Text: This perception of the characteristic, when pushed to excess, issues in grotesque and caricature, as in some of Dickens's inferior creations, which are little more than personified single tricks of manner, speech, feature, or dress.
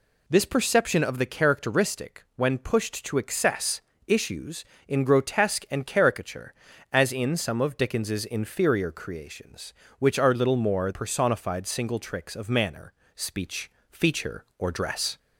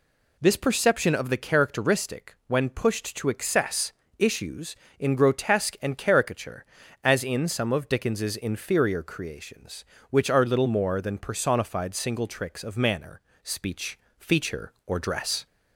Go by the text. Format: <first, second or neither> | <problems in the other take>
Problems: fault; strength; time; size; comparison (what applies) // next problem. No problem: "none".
second | skips "than"; at 10.9 s